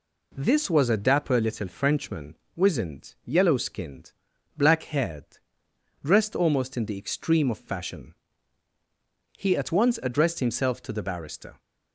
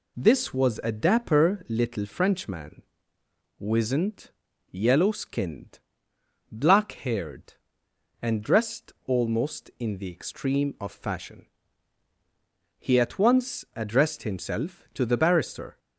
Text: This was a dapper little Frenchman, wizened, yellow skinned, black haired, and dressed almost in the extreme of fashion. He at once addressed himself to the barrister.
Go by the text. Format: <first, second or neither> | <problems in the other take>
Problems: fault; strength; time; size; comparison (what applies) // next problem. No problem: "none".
second | skips "and"; at 5.6 s